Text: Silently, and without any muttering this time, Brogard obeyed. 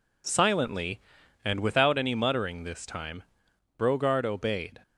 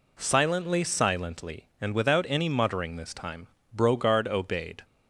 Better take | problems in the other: first | says "Silently" twice; at 0.8 s

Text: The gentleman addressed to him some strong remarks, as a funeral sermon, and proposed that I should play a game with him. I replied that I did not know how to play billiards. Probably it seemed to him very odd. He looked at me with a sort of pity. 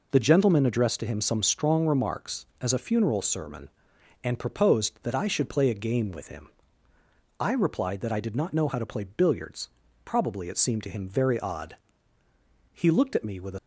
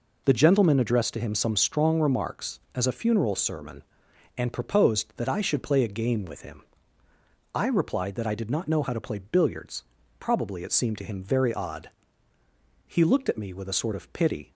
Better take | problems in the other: second | stops before "sort of pity"; at 13.5 s

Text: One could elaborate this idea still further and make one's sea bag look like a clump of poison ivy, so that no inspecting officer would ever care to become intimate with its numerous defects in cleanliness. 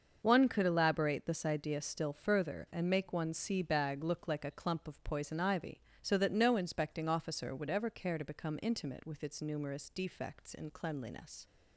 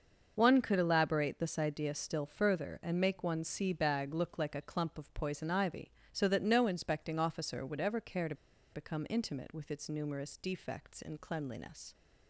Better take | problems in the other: first | starts louder than the rest; until 1.3 s; 6.5 dB; also in the first // pauses between "to" and "become"; at 8.3 s; 0.39 s long

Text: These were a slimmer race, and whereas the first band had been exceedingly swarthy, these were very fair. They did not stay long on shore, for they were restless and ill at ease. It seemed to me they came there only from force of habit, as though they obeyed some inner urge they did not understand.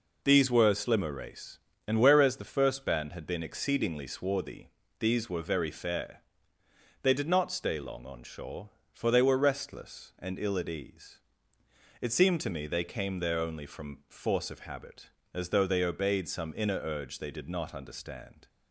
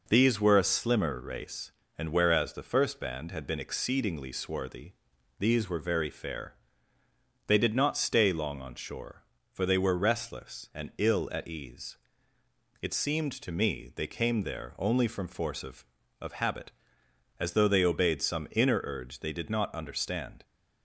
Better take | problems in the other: first | says "of" twice; at 16.2 s

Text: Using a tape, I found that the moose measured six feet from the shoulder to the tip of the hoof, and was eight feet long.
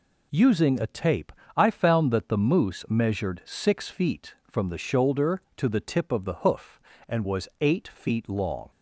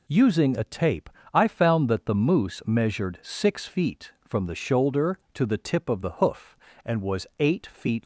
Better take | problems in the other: first | stops before "long"; at 8.0 s

